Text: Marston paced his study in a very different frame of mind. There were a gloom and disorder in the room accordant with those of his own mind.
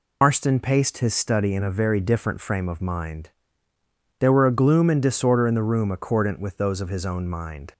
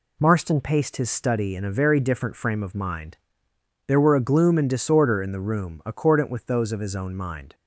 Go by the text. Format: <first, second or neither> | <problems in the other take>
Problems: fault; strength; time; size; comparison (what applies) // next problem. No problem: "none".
second | loses the start of "Marston"; at 0.2 s; 130 ms